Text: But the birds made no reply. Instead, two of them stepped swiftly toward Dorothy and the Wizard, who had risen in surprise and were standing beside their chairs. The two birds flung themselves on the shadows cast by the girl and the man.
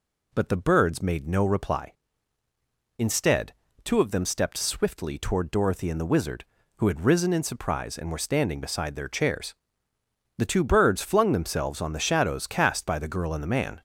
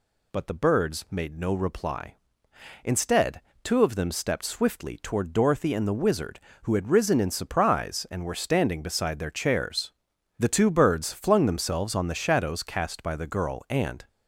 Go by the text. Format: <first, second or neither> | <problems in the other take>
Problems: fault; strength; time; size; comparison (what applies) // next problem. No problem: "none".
first | stops before "the man"; at 14.0 s